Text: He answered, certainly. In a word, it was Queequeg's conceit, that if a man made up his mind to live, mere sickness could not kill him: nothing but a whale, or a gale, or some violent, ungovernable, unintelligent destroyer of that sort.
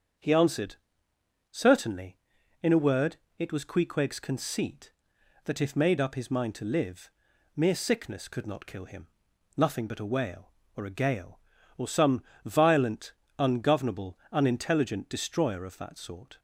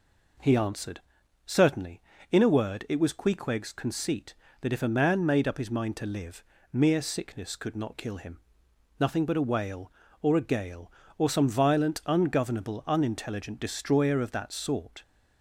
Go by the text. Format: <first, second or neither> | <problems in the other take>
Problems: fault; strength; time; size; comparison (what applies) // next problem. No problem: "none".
second | starts louder than the rest; strong; until 1.9 s; 7 dB // skips "a man"; at 5.7 s // pauses between "some" and "violent"; slight; at 12.2 s; 0.24 s long